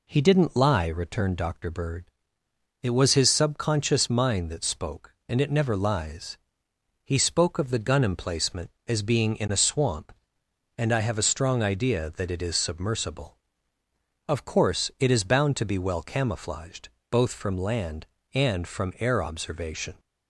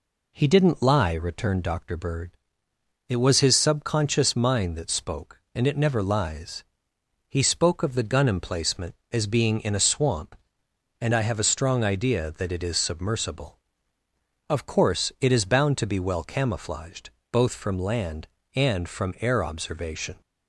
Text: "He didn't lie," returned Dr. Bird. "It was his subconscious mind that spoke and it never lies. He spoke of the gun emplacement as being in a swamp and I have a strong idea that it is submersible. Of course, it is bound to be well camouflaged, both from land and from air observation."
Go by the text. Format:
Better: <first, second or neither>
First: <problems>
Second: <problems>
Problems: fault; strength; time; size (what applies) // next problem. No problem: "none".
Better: neither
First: none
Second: none